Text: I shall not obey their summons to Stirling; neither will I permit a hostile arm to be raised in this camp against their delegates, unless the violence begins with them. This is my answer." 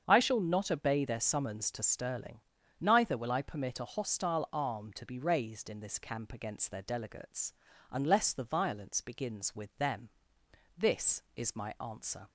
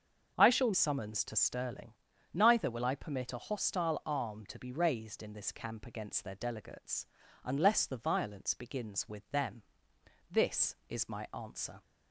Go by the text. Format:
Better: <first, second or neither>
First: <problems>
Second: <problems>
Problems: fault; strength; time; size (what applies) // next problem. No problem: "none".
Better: first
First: starts louder than the rest; strong; until 1.0 s; 7.5 dB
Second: starts louder than the rest; until 1.3 s; 6.5 dB // skips "not obey their"; at 0.7 s